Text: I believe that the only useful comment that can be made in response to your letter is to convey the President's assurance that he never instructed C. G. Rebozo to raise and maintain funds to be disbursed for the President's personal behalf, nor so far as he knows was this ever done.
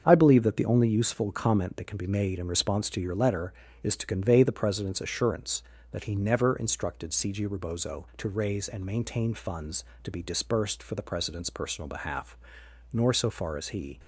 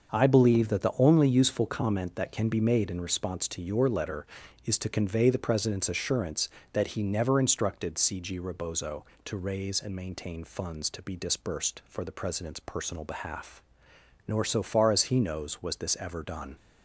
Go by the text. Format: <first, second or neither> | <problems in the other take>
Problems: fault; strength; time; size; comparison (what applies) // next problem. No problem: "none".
second | starts louder than the rest; until 1.0 s; 7 dB; also in the second // stops before "knows was this ever done"; at 13.9 s